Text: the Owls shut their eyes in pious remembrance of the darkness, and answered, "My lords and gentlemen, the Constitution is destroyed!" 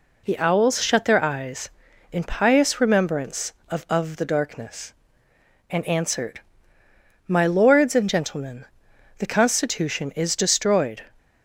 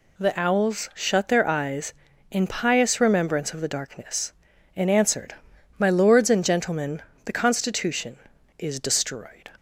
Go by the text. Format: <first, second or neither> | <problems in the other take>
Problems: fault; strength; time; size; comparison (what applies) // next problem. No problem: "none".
second | says "of" twice; at 3.8 s